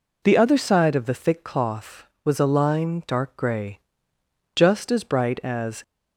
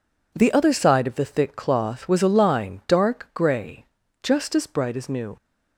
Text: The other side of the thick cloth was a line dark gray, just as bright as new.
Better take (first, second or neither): second